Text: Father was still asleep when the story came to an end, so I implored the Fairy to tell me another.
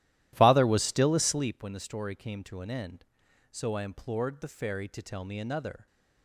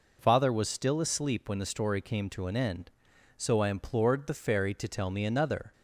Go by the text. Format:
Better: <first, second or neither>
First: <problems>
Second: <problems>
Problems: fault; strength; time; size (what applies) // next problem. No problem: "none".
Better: second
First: starts louder than the rest; strong; until 1.6 s; 14 dB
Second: none